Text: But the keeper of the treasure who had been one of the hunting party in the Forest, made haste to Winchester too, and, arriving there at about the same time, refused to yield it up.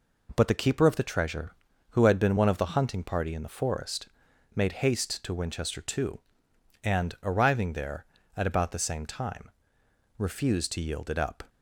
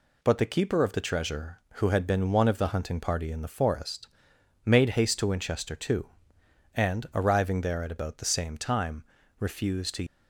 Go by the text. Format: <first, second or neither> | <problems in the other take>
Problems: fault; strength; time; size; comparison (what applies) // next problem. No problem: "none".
first | stops before "yield it up"; at 10.0 s